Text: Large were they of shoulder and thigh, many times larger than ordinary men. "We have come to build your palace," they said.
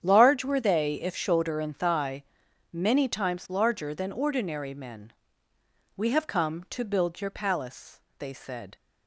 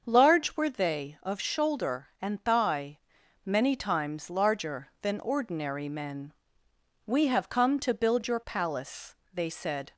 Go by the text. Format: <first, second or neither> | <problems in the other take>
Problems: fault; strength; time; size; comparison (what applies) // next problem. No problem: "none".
second | starts louder than the rest; strong; until 1.0 s; 8.5 dB; also in the second // says "if" for "of"; at 1.0 s